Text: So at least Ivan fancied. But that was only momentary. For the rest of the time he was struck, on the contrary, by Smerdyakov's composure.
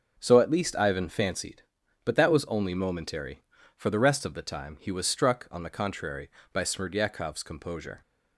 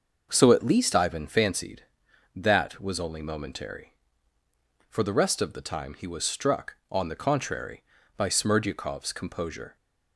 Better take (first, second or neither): first